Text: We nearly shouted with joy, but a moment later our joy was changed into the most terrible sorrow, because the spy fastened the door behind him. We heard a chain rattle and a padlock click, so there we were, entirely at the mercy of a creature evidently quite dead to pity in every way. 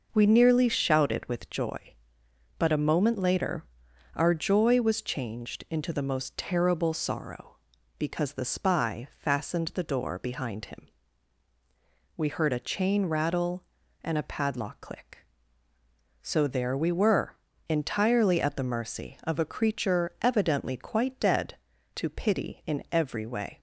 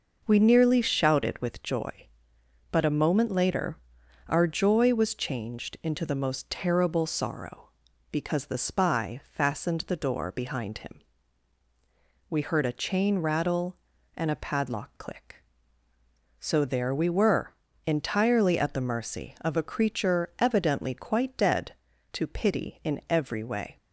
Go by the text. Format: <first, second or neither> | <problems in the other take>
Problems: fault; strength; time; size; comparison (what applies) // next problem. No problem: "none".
neither | pauses between "later" and "our"; noticeable; the same in both